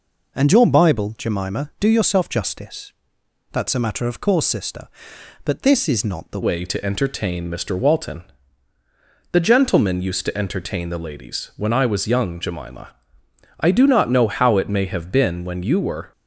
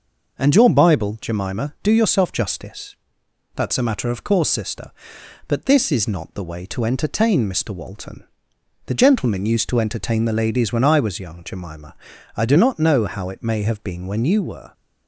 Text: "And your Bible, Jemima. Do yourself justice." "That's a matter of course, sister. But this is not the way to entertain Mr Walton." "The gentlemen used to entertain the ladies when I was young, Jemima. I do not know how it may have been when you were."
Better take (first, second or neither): second